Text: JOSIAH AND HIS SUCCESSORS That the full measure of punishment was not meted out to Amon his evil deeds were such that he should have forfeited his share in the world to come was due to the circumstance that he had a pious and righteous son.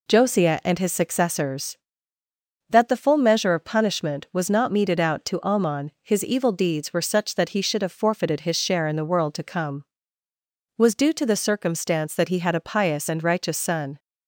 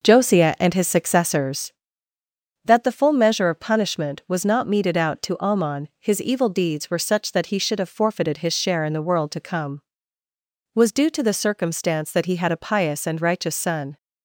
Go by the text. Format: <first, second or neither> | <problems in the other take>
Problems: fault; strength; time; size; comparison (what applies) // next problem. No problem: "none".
first | starts louder than the rest; noticeable; until 1.7 s; 5.5 dB